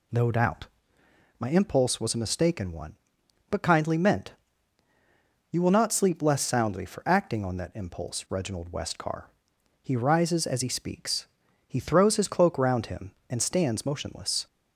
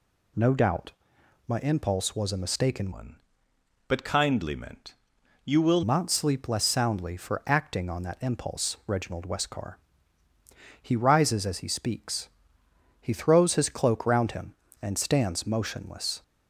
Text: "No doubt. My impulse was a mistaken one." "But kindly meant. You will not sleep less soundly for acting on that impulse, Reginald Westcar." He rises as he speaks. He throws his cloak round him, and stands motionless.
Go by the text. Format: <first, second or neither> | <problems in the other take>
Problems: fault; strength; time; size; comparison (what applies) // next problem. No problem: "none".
first | changes voice from "one" to "will"; from 2.9 to 5.8 s; 2.9 s long